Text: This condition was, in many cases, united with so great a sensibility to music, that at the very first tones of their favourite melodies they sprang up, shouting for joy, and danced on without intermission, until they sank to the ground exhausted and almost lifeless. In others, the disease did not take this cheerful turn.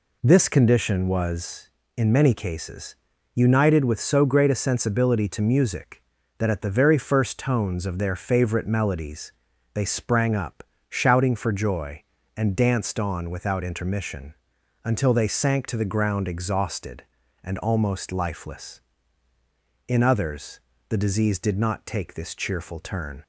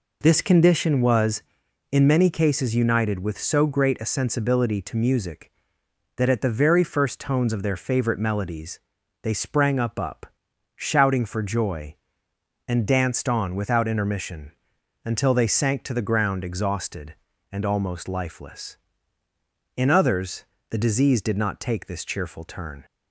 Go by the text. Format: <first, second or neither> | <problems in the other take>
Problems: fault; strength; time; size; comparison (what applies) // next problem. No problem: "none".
first | pauses between "melodies" and "they"; at 8.7 s; 0.42 s long; also in the first // says "up" twice; at 9.9 s